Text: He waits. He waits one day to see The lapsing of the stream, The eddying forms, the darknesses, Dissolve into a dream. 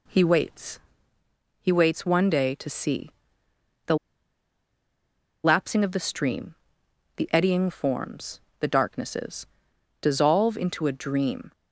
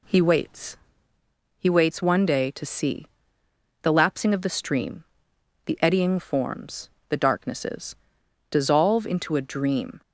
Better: second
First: pauses between "see" and "The"; noticeable; at 3.0 s; 0.76 s long // pauses between "The" and "lapsing"; strong; at 3.9 s; 1.4 s long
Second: pauses between "see" and "The"; noticeable; at 3.0 s; 0.76 s long

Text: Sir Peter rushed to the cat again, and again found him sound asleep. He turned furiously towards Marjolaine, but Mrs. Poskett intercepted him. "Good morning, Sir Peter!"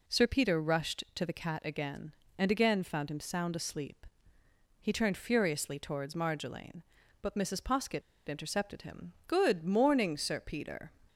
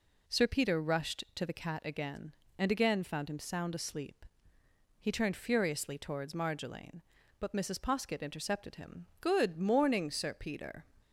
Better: second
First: pauses between "Poskett" and "intercepted"; slight; at 8.0 s; 0.26 s long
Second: none

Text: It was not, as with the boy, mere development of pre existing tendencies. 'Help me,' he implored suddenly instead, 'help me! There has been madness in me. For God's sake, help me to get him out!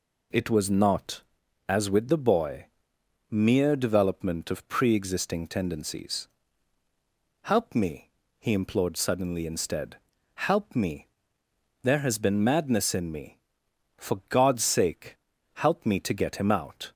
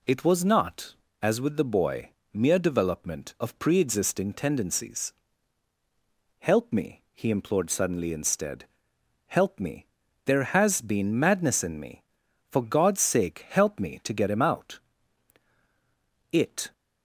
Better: first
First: none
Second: goes on to say "It"; slight; from 16.3 s on; 0.40 s long

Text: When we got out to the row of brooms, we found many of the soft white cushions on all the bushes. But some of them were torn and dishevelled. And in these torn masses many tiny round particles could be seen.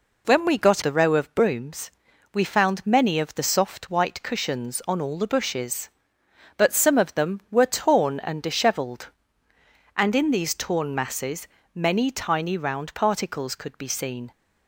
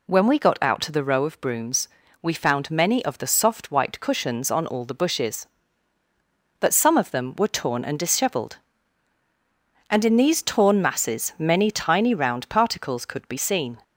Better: second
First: skips "out to"; at 0.8 s // pauses between "masses" and "many"; slight; at 11.4 s; 0.26 s long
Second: none

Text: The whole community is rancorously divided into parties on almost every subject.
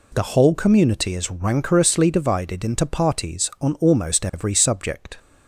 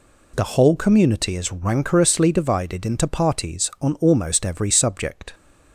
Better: neither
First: none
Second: none

